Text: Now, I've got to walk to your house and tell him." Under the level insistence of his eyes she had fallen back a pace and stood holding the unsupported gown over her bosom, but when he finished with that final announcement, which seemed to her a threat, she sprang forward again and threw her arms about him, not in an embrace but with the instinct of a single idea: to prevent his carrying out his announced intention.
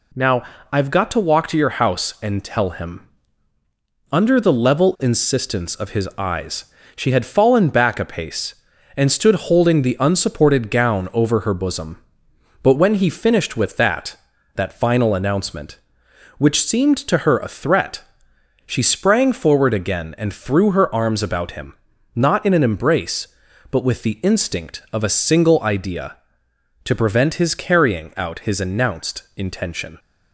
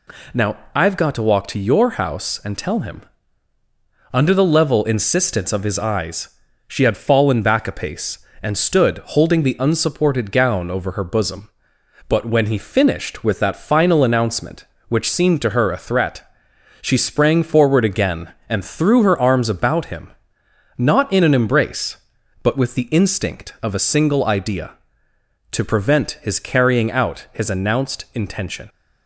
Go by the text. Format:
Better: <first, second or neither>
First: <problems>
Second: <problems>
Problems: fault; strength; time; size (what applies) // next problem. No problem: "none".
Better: second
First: pauses between "eyes" and "she"; slight; at 6.6 s; 0.30 s long // says "that" twice; at 14.5 s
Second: pauses between "eyes" and "she"; at 6.2 s; 0.38 s long